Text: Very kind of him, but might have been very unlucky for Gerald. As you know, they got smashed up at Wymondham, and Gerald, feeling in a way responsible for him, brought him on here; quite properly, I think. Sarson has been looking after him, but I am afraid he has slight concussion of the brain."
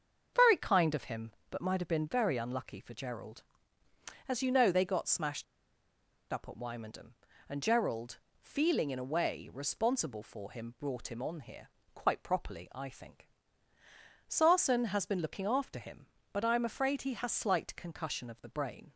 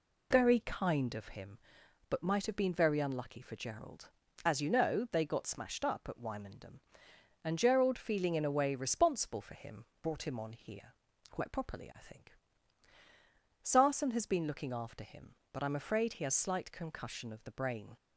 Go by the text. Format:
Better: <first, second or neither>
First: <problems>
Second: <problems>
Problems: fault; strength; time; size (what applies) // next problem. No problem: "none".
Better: second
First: starts louder than the rest; until 1.5 s; 6.5 dB // pauses between "smashed" and "up"; noticeable; at 5.4 s; 0.88 s long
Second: none